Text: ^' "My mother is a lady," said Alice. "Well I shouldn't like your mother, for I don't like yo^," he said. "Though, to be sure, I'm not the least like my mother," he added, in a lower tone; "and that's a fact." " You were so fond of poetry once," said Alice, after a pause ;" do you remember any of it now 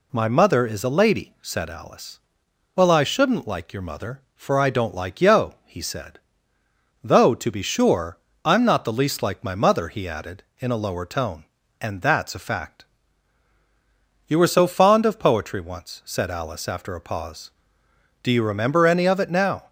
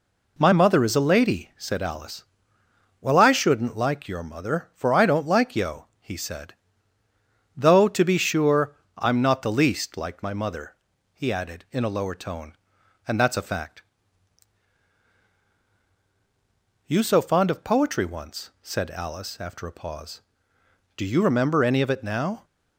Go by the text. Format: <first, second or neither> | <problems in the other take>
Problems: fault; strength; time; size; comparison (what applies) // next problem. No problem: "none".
first | skips "were"; at 17.0 s